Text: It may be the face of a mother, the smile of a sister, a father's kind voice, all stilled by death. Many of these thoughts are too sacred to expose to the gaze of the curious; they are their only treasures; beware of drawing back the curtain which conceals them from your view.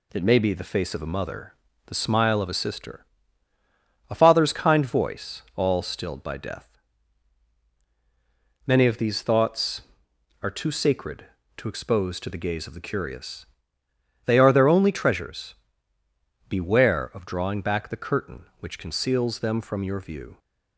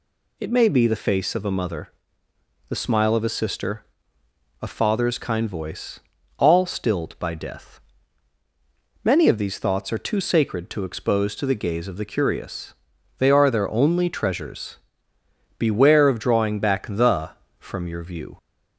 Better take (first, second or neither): first